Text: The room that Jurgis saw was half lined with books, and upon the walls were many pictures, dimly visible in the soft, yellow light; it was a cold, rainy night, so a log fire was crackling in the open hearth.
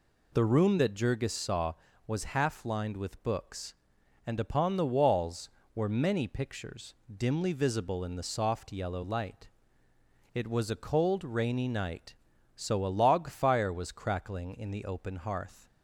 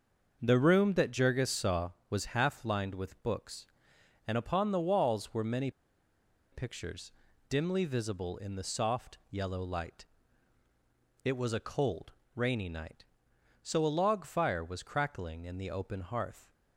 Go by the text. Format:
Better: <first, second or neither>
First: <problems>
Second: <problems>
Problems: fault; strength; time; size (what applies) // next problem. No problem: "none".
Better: first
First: none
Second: starts louder than the rest; until 1.4 s; 6 dB // pauses between "many" and "pictures"; noticeable; at 5.6 s; 0.82 s long